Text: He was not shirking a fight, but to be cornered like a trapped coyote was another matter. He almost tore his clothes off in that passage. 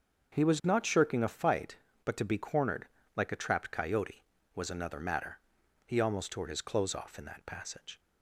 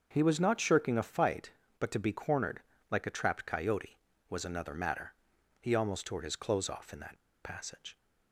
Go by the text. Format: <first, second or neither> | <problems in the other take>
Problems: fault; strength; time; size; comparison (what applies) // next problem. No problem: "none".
first | starts louder than the rest; until 1.1 s; 6.5 dB; also in the first // pauses between "cornered" and "like"; slight; at 2.6 s; 0.28 s long; slight in the first // pauses between "that" and "passage"; slight; at 7.2 s; 0.23 s long